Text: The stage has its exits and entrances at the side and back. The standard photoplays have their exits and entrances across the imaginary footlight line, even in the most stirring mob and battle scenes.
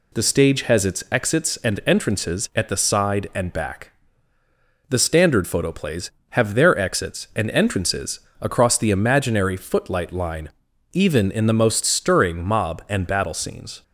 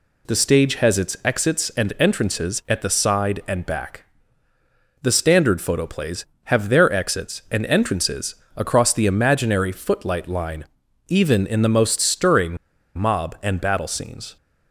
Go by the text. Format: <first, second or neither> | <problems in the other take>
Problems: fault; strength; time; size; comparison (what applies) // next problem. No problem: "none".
first | pauses between "entrances" and "across"; slight; at 8.3 s; 0.22 s long; slight in the first // pauses between "stirring" and "mob"; at 12.5 s; 0.41 s long